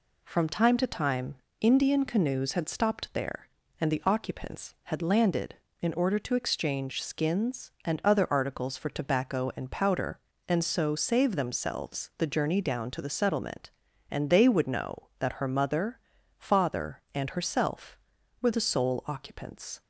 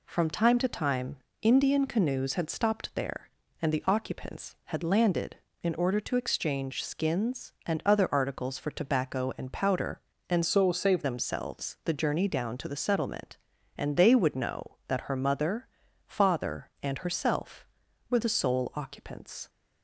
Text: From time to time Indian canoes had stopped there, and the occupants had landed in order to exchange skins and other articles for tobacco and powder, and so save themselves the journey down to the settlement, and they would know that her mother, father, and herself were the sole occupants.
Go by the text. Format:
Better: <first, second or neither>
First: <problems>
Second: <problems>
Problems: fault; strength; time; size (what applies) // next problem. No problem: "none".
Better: first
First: pauses between "time" and "Indian"; slight; at 1.3 s; 0.24 s long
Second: pauses between "time" and "Indian"; slight; at 1.1 s; 0.24 s long // changes voice from "so" to "save"; from 10.4 to 11.0 s; 0.6 s long